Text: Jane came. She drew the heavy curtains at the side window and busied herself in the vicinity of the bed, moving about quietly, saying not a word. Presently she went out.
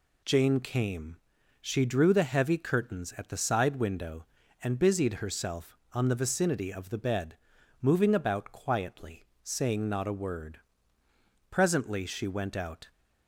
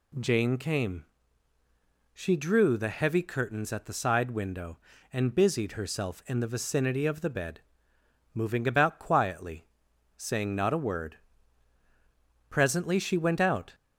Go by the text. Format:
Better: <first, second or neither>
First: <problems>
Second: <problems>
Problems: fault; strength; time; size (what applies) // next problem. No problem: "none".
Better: second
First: says "on" for "in"; at 5.9 s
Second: none